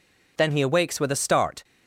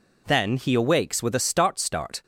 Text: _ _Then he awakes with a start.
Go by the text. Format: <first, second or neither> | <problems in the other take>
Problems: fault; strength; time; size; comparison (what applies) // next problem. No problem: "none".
first | says "start" twice; at 1.7 s